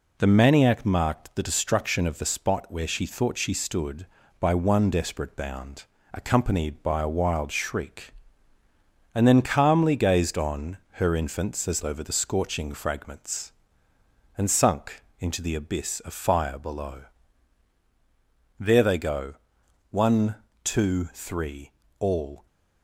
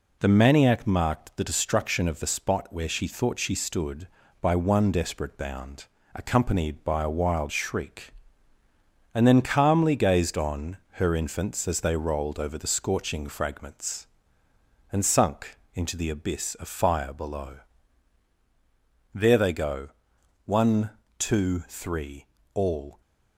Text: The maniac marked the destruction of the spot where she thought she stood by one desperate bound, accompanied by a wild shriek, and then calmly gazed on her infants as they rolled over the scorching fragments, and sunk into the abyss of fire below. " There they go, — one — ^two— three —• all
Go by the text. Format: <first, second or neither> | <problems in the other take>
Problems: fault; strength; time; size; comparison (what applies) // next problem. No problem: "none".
second | pauses between "on" and "her"; slight; at 10.7 s; 0.24 s long; slight in the second // skips "they rolled"; at 11.8 s // pauses between "sunk" and "into"; slight; at 15.0 s; 0.16 s long; slight in the second